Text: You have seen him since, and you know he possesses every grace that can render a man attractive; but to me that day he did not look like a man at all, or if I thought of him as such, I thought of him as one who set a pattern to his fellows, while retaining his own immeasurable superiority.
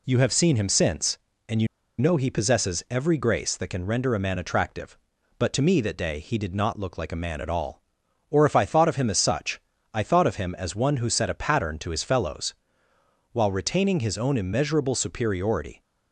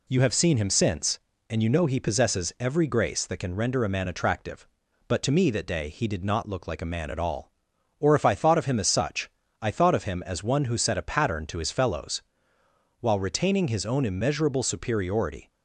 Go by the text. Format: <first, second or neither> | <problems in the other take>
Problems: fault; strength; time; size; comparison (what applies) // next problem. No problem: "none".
second | pauses between "you" and "know"; slight; at 1.6 s; 0.32 s long